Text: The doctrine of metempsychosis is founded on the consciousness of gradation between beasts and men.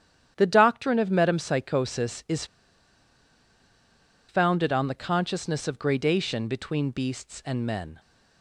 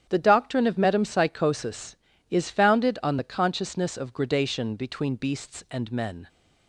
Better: second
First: starts louder than the rest; strong; until 1.3 s; 10.5 dB // pauses between "is" and "founded"; strong; at 2.4 s; 1.8 s long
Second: starts louder than the rest; strong; until 1.1 s; 10 dB

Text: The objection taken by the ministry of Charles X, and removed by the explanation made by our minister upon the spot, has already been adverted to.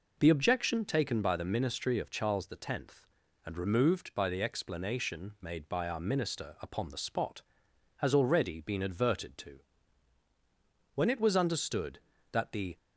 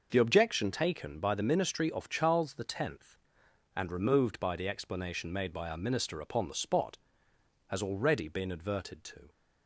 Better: second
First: goes on to say "When it was understood that the"; strong; from 10.9 s on; 1.8 s long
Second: none

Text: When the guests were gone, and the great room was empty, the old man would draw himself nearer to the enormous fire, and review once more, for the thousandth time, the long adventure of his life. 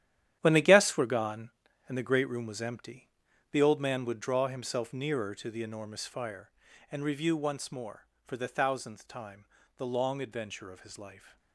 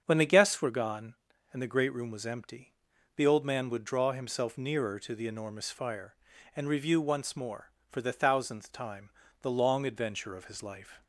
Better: second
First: gets quieter; strong; throughout; 11.5 dB // starts louder than the rest; strong; until 1.4 s; 11 dB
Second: starts louder than the rest; until 1.0 s; 7 dB

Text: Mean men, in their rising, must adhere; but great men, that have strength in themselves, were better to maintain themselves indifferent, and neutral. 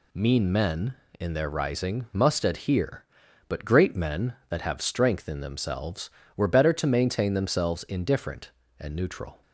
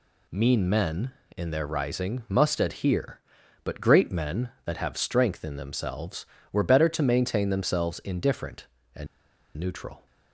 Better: first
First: none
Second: pauses between "and" and "neutral"; noticeable; at 9.0 s; 0.50 s long

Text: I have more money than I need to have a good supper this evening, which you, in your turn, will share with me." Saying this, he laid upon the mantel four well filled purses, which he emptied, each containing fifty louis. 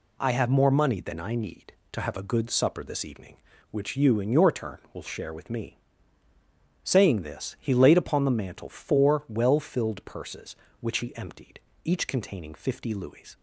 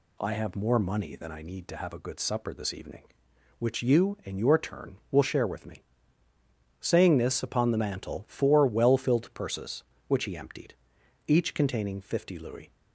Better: first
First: none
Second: skips "he laid"; at 7.4 s

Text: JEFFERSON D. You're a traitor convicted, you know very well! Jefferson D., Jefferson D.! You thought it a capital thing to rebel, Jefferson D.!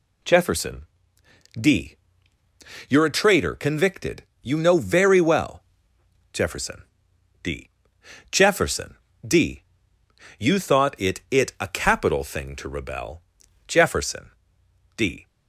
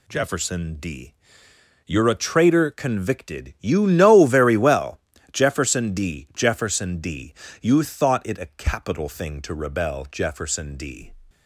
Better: second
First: pauses between "JEFFERSON" and "D"; noticeable; at 0.8 s; 0.74 s long // pauses between "Jefferson" and "D"; noticeable; at 6.8 s; 0.60 s long // pauses between "Jefferson" and "D"; slight; at 8.9 s; 0.32 s long // says "it" twice; at 11.3 s // pauses between "Jefferson" and "D"; noticeable; at 14.3 s; 0.66 s long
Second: none

